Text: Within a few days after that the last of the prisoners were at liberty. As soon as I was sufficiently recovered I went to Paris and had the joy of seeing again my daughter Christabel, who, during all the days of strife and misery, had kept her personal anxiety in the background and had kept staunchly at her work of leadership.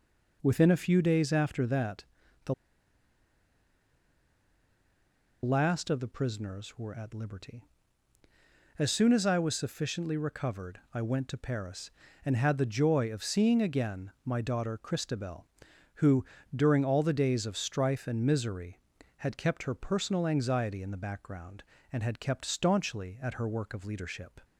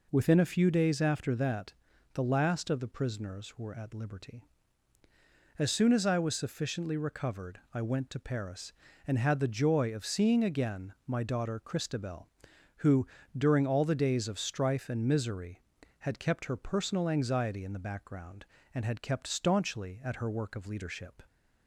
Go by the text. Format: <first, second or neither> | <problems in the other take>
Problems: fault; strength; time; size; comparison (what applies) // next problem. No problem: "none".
second | pauses between "that" and "the"; at 2.0 s; 0.40 s long; also in the second // pauses between "the" and "last"; strong; at 2.5 s; 2.8 s long // pauses between "recovered" and "I"; slight; at 10.7 s; 0.16 s long; slight in the second // pauses between "again" and "my"; slight; at 14.0 s; 0.16 s long; slight in the second